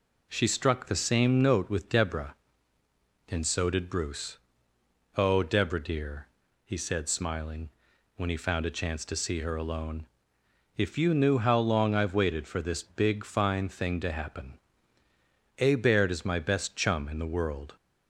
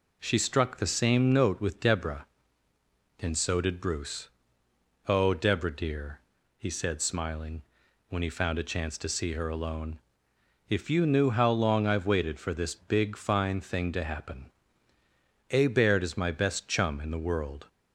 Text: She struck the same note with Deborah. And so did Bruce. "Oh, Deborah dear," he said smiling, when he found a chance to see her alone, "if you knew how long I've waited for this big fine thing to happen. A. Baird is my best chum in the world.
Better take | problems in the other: neither | none

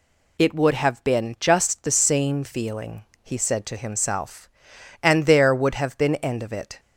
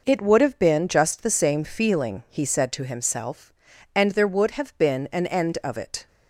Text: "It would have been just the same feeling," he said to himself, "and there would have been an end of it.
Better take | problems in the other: second | skips "an"; at 6.1 s

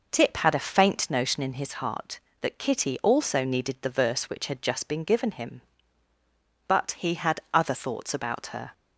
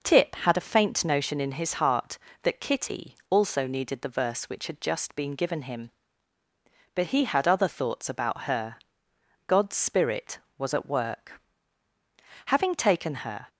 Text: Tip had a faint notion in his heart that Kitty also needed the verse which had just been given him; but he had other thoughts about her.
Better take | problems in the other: first | goes on to say "God's Spirit was at work Having taken her"; strong; from 9.4 s on; 4.0 s long

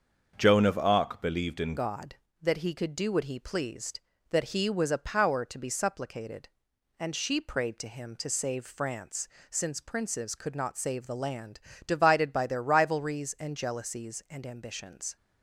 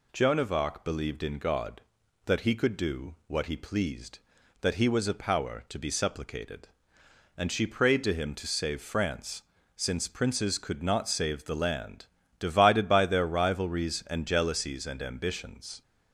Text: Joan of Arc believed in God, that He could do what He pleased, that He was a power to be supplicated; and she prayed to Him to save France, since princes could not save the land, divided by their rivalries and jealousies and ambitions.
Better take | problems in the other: second | starts louder than the rest; until 1.3 s; 7 dB // changes voice at "God"; from 1.7 s on; 13.4 s long

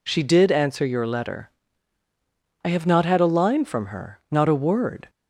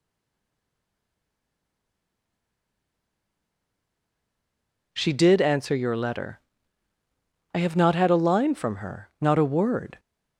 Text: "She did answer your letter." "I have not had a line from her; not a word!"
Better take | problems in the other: first | stays silent before the first word; strong; until 4.9 s; 4.9 s long

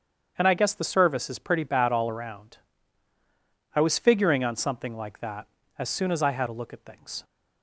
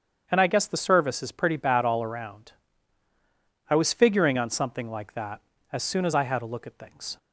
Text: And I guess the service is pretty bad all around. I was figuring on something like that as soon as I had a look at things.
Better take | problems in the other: neither | starts louder than the rest; strong; the same in both

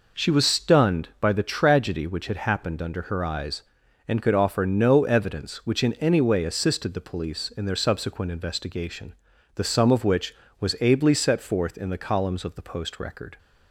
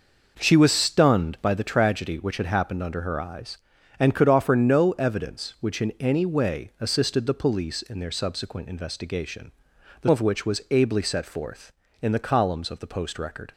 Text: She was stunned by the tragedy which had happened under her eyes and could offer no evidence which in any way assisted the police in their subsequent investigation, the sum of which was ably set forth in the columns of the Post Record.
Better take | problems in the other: first | skips "sum"; at 10.0 s

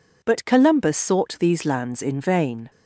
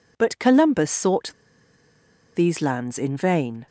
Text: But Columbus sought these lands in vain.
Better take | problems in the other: first | pauses between "sought" and "these"; at 1.3 s; 1.0 s long

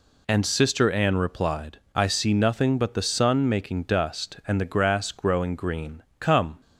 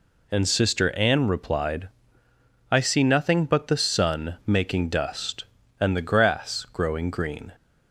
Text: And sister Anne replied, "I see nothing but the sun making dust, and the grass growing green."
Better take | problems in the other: second | goes on to say "Come"; slight; from 6.1 s on; 0.42 s long

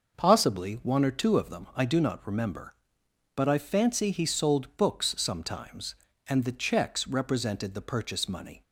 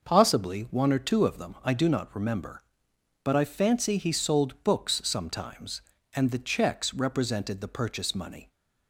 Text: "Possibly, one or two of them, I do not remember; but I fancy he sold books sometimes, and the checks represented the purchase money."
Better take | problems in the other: neither | none

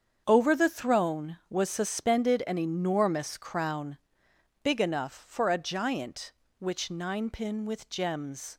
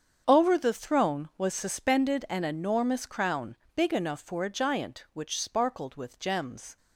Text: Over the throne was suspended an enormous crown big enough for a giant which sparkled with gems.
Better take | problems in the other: second | starts louder than the rest; strong; until 1.2 s; 7.5 dB; strong in the second // pauses between "crown" and "big"; noticeable; at 3.9 s; 0.64 s long; slight in the second // says "ninepin" for "sparkled"; at 6.9 s

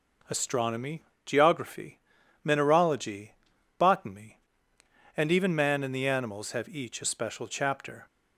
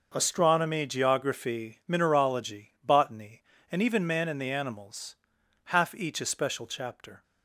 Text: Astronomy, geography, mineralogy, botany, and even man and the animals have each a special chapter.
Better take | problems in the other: first | says "half" for "have"; at 5.6 s

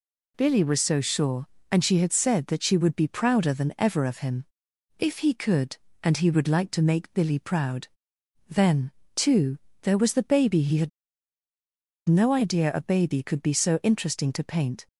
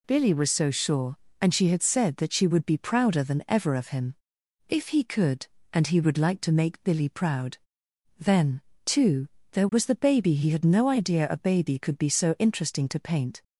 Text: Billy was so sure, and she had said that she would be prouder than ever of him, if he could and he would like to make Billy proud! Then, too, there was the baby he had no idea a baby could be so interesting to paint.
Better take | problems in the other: second | pauses between "had" and "no"; at 10.8 s; 1.1 s long

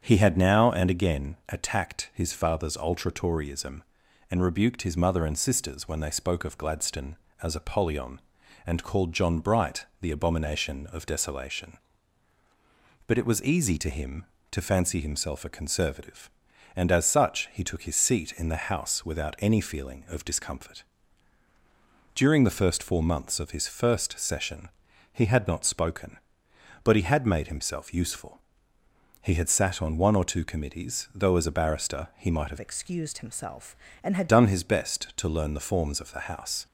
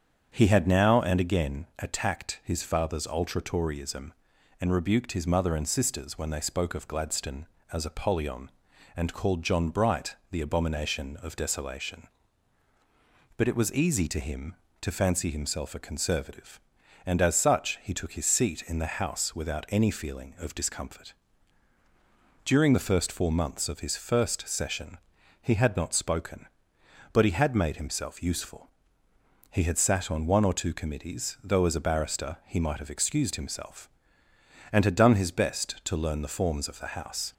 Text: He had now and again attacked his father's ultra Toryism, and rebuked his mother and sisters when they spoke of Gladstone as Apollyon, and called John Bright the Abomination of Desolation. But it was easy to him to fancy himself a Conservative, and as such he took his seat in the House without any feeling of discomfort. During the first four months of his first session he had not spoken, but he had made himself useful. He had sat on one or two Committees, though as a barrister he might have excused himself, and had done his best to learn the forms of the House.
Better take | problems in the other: second | starts louder than the rest; strong; until 1.0 s; 7.5 dB; strong in the second // pauses between "Bright" and "the"; slight; at 9.8 s; 0.16 s long; slight in the second // pauses between "session" and "he"; noticeable; at 24.6 s; 0.46 s long; noticeable in the second // changes voice from "excused" to "had"; from 32.5 to 34.2 s; 1.7 s long

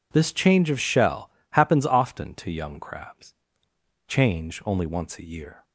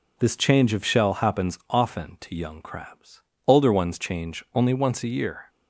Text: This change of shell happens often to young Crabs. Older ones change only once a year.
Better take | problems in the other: second | pauses between "shell" and "happens"; slight; at 1.2 s; 0.22 s long // skips "Older ones"; at 3.7 s

